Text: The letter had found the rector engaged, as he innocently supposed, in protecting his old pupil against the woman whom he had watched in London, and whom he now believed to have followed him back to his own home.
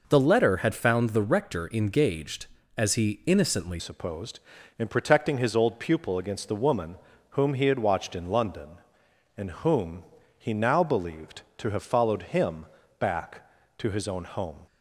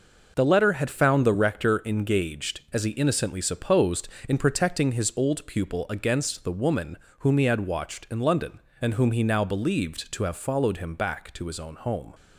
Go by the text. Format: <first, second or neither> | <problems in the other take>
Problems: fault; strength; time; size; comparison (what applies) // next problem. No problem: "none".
second | changes voice at "supposed"; from 3.7 s on; 10.9 s long // pauses between "woman" and "whom"; slight; at 6.9 s; 0.34 s long; slight in the second // pauses between "whom" and "he"; slight; at 10.0 s; 0.34 s long // pauses between "him" and "back"; slight; at 12.6 s; 0.34 s long